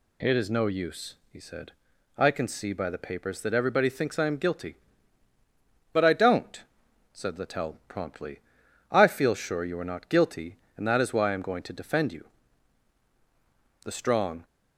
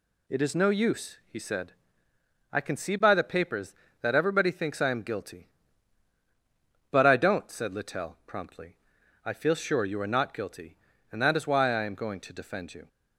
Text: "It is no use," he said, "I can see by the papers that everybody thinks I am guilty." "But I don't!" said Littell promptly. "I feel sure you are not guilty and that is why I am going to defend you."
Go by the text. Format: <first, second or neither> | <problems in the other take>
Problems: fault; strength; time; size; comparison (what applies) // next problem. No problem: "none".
second | goes on to say "The strong"; from 13.8 s on; 0.58 s long